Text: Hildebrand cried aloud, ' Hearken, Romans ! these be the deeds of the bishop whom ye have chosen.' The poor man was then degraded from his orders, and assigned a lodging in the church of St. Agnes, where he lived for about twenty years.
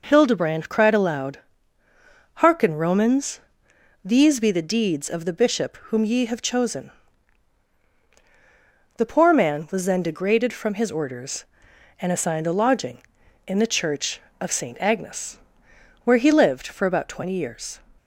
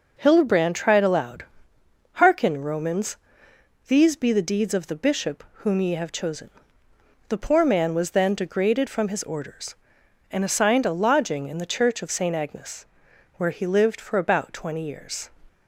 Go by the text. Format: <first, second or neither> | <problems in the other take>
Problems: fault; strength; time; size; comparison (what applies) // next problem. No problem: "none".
first | says "tried" for "cried"; at 0.7 s